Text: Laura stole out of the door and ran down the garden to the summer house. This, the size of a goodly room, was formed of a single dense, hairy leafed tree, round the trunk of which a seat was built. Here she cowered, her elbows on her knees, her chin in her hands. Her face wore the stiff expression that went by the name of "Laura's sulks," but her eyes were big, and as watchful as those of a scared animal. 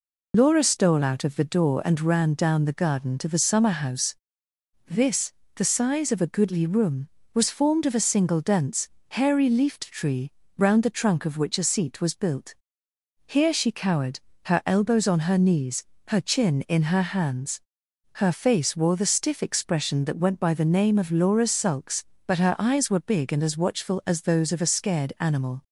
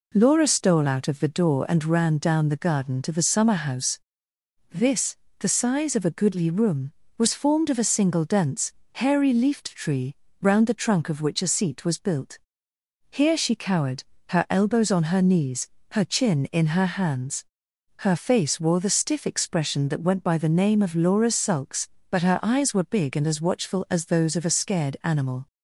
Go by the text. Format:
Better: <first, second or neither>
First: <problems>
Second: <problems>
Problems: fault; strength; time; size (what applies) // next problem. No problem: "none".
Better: second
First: loses the start of "Laura"; at 0.3 s; 45 ms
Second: none